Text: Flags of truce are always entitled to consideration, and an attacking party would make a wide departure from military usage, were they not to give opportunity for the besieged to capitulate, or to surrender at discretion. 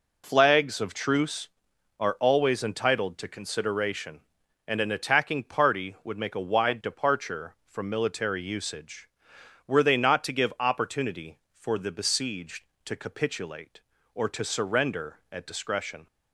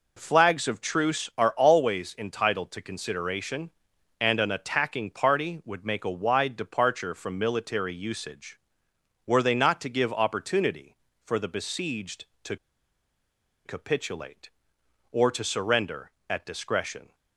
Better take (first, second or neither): first